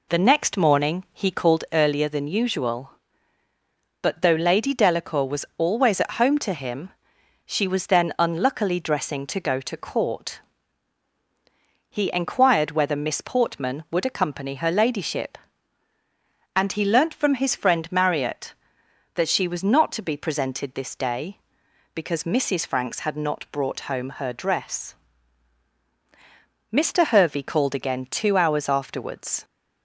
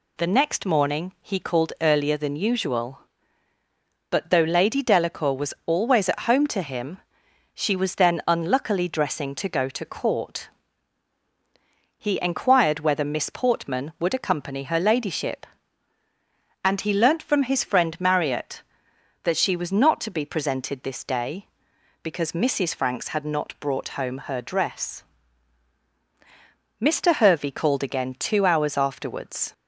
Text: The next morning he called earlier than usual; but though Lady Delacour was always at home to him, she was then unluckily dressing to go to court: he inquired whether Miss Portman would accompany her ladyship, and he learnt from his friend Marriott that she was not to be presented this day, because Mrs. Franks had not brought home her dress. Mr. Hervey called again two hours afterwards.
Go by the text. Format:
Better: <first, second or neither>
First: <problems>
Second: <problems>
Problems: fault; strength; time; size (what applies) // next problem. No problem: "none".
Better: second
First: starts louder than the rest; slight; until 1.7 s; 3 dB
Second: none